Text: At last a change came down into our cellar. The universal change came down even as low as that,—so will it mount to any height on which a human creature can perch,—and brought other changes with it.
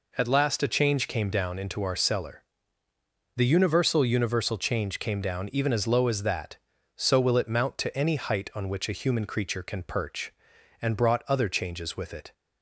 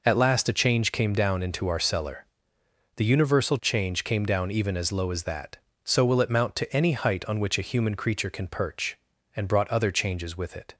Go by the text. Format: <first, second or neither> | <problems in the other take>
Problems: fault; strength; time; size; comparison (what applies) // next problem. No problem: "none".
second | says "universal" twice; at 4.0 s